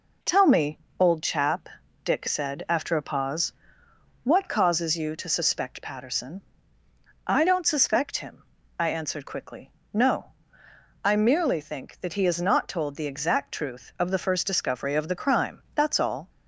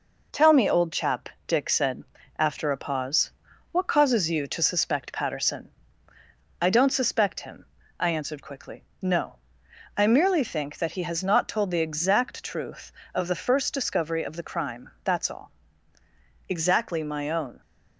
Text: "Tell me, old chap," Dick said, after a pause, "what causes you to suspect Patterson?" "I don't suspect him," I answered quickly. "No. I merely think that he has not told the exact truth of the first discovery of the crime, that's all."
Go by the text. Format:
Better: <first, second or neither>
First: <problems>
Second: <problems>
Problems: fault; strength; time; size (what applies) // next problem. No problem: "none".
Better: first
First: none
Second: goes on to say "Exactly my own"; noticeable; from 16.4 s on; 1.1 s long